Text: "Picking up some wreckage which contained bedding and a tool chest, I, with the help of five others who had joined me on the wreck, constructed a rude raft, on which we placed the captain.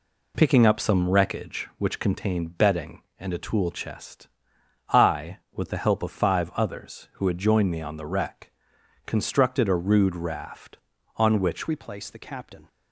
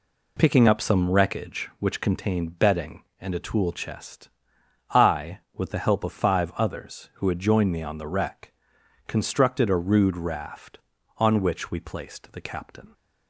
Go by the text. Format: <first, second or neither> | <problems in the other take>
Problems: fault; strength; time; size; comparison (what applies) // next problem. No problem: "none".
second | changes voice at "we"; from 11.6 s on; 1.0 s long